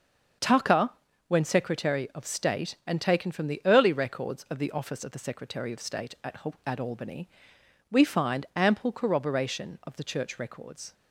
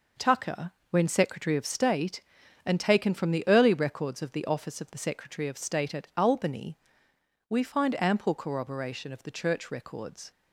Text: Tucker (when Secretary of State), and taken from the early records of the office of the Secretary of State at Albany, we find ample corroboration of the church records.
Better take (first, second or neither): second